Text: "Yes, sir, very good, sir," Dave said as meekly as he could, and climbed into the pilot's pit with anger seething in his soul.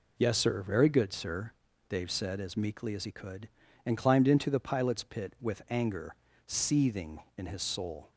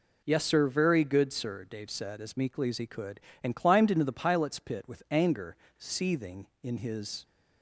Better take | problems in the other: first | pauses between "anger" and "seething"; slight; at 5.5 s; 0.22 s long; slight in the first // stops before "soul"; at 7.2 s

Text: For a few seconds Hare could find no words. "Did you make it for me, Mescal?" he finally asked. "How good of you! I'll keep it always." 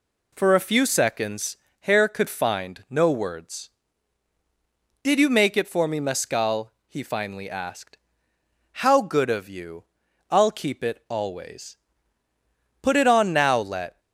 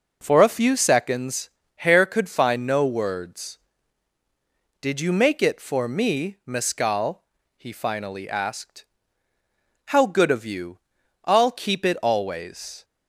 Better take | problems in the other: second | pauses between "seconds" and "Hare"; slight; at 1.5 s; 0.24 s long; slight in the second // goes on to say "Put it on now let"; noticeable; from 12.8 s on; 1.1 s long

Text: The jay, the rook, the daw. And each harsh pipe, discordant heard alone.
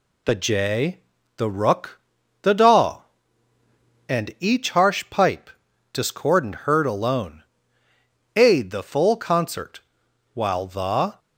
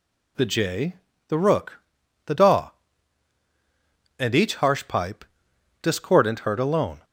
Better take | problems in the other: second | goes on to say "Aid the full concert While the"; strong; from 8.3 s on; 2.8 s long

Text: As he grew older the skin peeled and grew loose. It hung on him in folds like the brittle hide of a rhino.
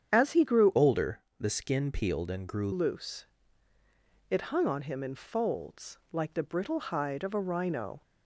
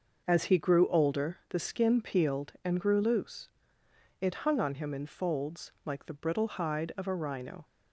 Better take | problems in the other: second | starts louder than the rest; strong; until 1.1 s; 8.5 dB; also in the second // changes voice from "older" to "grew"; from 0.7 to 2.7 s; 2.0 s long // pauses between "older" and "the"; slight; at 1.2 s; 0.18 s long // pauses between "folds" and "like"; slight; at 5.9 s; 0.16 s long

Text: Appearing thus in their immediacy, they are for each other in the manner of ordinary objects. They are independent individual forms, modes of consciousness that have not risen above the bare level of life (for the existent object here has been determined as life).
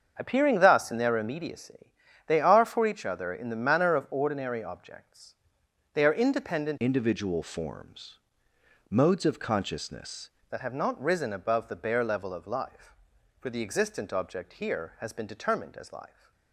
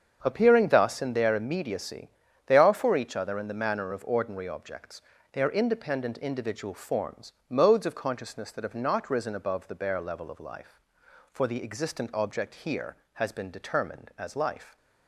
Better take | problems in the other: second | starts louder than the rest; until 1.1 s; 7 dB; strong in the second // changes voice from "individual" to "consciousness"; from 6.8 to 10.3 s; 3.5 s long

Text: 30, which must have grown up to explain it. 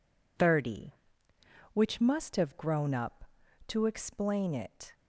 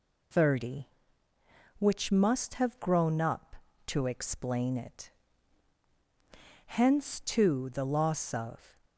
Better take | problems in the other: first | goes on to say "Hence too the loss of"; strong; from 6.6 s on; 2.1 s long

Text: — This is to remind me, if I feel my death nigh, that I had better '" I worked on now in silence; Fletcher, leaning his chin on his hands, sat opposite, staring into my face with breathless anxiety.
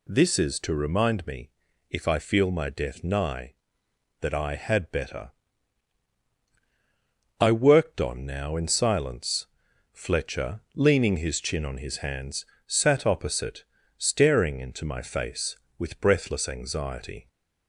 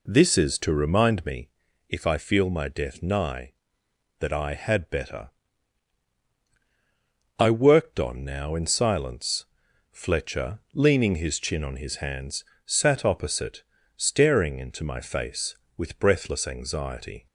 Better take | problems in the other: first | starts louder than the rest; until 1.5 s; 3.5 dB

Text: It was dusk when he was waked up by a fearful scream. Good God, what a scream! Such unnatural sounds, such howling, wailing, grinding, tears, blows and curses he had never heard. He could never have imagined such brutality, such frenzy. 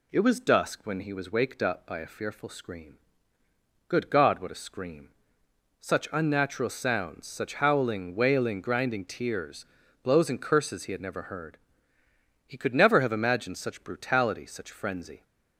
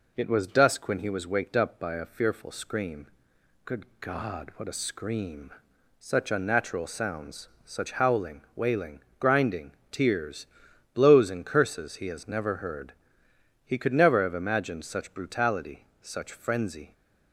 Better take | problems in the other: first | pauses between "Good" and "God"; slight; at 3.8 s; 0.16 s long // says "has" for "had"; at 12.0 s

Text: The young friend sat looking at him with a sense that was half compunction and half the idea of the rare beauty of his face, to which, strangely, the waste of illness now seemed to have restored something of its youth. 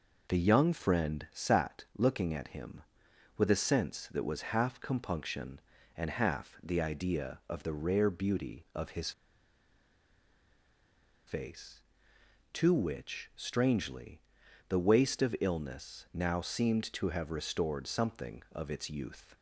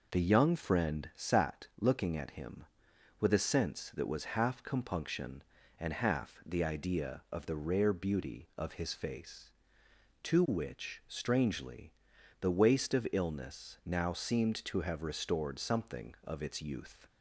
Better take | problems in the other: second | pauses between "his" and "face"; strong; at 9.1 s; 2.1 s long

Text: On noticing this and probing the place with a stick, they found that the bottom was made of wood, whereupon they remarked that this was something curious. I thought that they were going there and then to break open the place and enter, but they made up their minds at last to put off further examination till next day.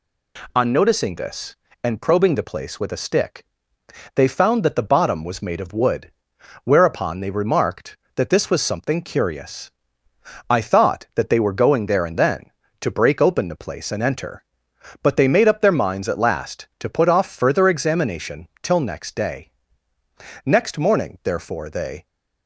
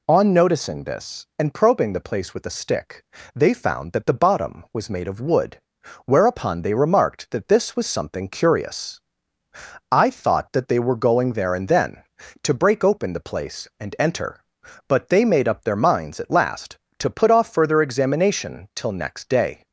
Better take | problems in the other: second | goes on to say "Next morning therefore they"; from 20.4 s on; 1.6 s long

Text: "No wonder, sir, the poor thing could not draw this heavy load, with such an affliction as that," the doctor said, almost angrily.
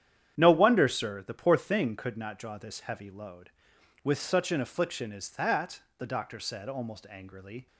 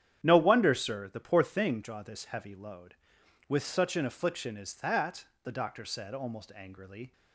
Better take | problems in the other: first | starts louder than the rest; strong; until 1.2 s; 9.5 dB; strong in the first // skips "could not"; at 1.8 s

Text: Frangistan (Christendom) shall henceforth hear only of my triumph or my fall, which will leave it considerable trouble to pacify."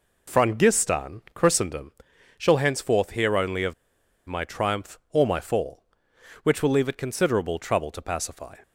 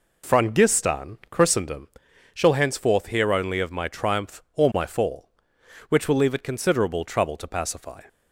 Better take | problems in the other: second | pauses between "of" and "my"; noticeable; at 3.7 s; 0.53 s long

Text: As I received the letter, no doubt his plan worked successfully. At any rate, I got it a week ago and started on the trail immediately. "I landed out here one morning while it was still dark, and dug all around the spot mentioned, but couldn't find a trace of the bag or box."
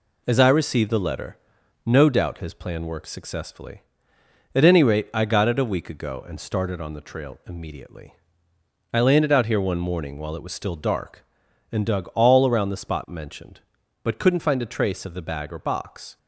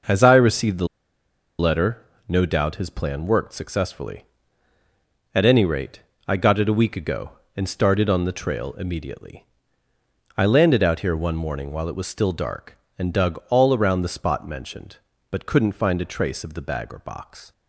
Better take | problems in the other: first | pauses between "the" and "letter"; noticeable; at 0.8 s; 0.72 s long

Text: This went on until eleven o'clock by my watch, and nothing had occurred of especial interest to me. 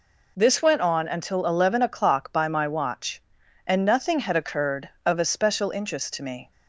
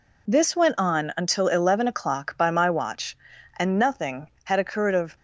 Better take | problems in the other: first | stops before "especial interest to me"; at 5.1 s

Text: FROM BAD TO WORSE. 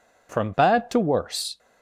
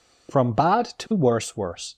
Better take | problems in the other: first | says "WORSE" twice; at 1.5 s

